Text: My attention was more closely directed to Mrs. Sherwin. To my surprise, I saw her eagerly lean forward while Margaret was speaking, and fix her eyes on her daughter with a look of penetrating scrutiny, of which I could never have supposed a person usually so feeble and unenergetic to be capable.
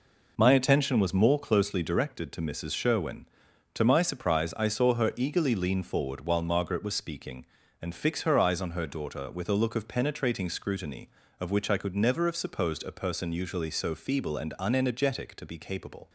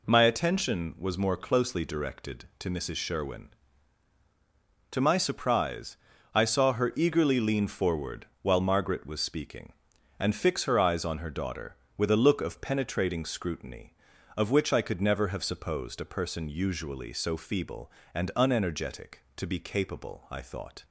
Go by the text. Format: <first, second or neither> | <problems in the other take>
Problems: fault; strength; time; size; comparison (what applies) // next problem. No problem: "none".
first | pauses between "forward" and "while"; slight; at 8.2 s; 0.16 s long // goes on to say "I thought"; from 20.2 s on; 0.56 s long